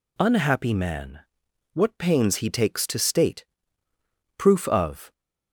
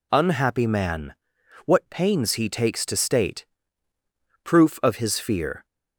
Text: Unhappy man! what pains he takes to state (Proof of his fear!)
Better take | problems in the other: second | stops before "his fear"; at 5.1 s

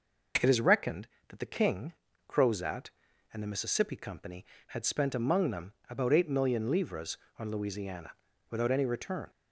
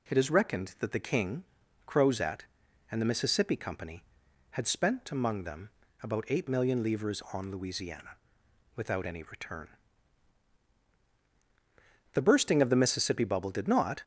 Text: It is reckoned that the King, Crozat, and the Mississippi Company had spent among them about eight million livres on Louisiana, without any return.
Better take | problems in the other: first | pauses between "them" and "about"; slight; at 5.6 s; 0.32 s long; slight in the first // goes on to say "The bursting of the Mississippi bubble did not"; strong; from 12.1 s on; 1.9 s long

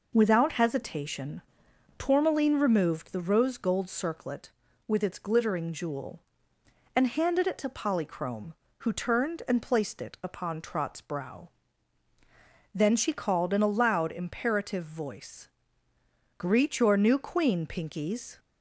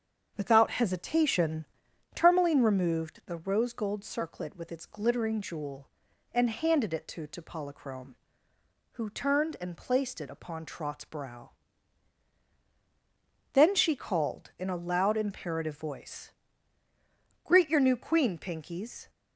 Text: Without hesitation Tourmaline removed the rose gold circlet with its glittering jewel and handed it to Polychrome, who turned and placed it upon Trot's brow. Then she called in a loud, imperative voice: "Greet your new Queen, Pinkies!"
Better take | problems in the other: first | starts louder than the rest; strong; until 1.3 s; 7 dB // pauses between "hesitation" and "Tourmaline"; noticeable; at 1.6 s; 0.50 s long; noticeable in the first // says "to" twice; at 7.2 s

